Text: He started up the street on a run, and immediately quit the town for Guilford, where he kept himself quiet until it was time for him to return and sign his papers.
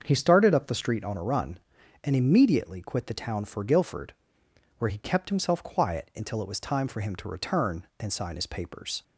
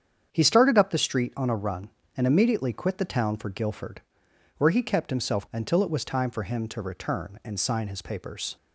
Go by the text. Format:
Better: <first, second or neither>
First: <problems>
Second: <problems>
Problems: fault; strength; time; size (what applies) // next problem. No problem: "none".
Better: first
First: starts louder than the rest; until 1.0 s; 7 dB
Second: starts louder than the rest; strong; until 1.3 s; 8 dB // skips "quiet"; at 5.4 s